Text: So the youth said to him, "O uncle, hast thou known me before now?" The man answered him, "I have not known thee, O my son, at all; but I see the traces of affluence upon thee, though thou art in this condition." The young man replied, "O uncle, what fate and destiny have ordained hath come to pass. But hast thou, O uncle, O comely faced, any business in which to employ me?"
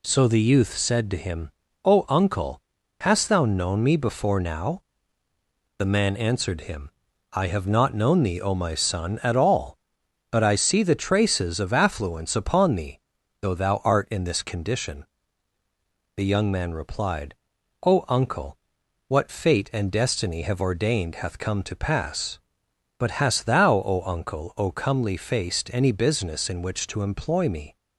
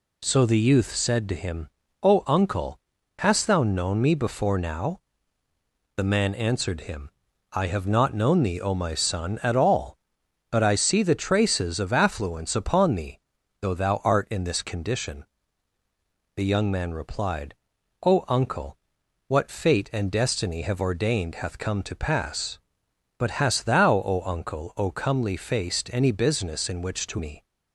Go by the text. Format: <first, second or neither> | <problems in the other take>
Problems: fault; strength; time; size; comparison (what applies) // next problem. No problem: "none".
first | skips "employ"; at 27.1 s